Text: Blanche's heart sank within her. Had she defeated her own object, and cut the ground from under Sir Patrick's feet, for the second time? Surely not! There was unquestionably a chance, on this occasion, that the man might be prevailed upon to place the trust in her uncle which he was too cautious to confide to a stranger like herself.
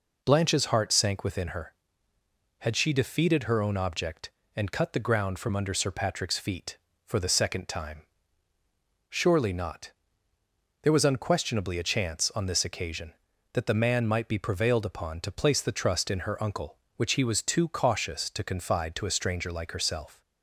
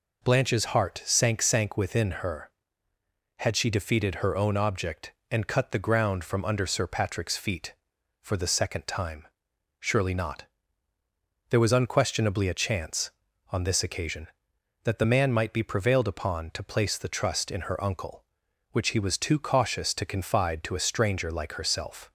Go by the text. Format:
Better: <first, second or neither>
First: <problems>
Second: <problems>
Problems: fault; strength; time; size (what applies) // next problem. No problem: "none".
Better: first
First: none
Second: says "sank" twice; at 1.4 s